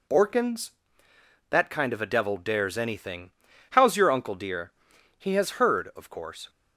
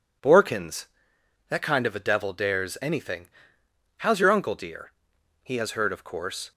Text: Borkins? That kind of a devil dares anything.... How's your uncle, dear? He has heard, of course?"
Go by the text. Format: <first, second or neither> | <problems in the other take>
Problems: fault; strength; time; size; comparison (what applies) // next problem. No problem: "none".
neither | none